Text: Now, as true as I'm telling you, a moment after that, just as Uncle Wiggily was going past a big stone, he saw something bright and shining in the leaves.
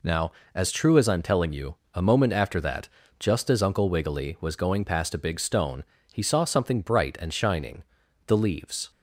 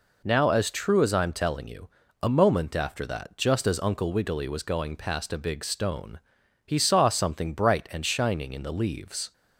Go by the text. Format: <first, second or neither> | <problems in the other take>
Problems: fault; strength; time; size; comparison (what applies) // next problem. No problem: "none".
second | skips "in"; at 8.0 s